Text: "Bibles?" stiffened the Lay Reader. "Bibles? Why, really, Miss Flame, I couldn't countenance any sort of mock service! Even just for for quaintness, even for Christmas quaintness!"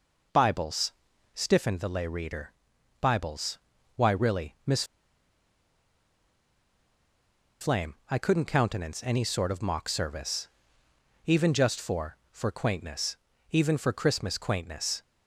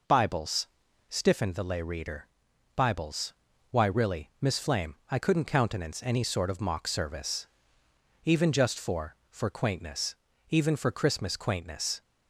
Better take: second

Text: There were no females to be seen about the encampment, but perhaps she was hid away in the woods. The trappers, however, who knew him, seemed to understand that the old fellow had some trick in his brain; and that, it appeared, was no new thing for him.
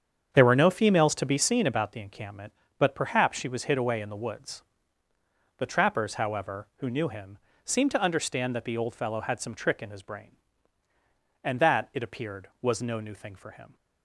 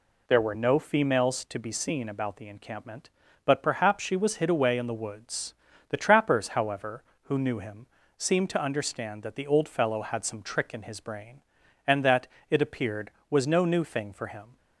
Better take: second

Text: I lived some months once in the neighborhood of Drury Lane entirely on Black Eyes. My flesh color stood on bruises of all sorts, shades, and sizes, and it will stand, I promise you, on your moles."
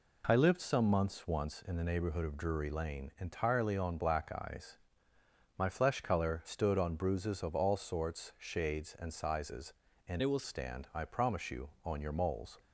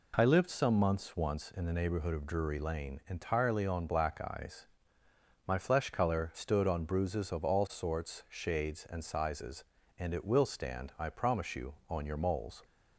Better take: second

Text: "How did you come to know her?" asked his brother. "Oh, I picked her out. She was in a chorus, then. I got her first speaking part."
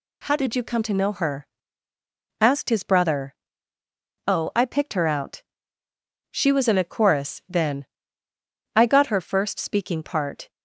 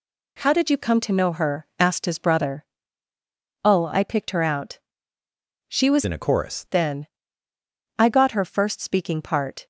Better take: first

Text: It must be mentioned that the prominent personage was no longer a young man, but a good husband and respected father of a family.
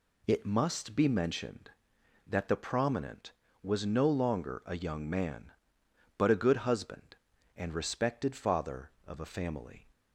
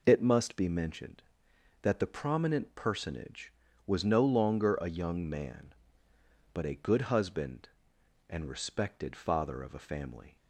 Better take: second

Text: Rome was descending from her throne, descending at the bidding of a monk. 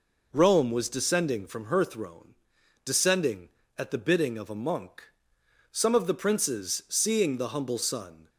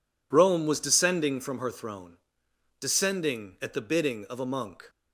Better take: second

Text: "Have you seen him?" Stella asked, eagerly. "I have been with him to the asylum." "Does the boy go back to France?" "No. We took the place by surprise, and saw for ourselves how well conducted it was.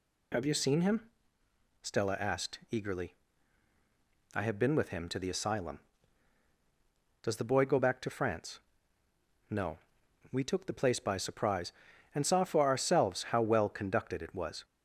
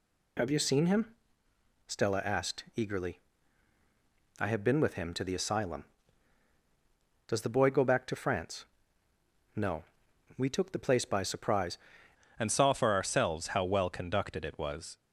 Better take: first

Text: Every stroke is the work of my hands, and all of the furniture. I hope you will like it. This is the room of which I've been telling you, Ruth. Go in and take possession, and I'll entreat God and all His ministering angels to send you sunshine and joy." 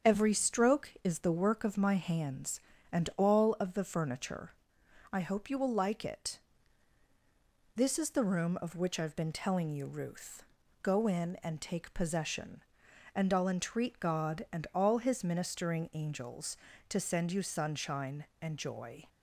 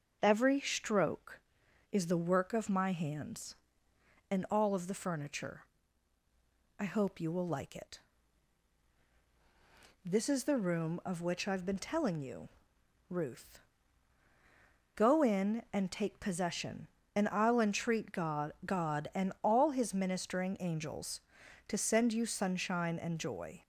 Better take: first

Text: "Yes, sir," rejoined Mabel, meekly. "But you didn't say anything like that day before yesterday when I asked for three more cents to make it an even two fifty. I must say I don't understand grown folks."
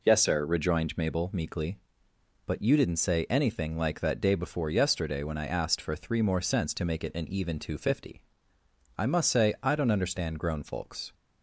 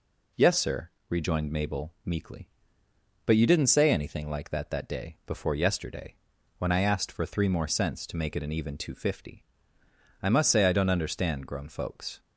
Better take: first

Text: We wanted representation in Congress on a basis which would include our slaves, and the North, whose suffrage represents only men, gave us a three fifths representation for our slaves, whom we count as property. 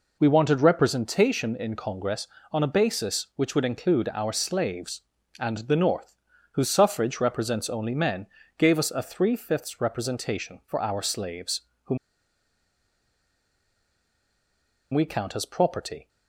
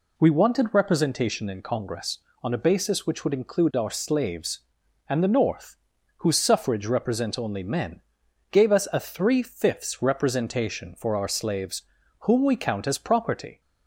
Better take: second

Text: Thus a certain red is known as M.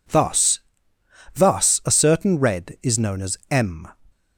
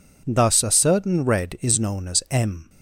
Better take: second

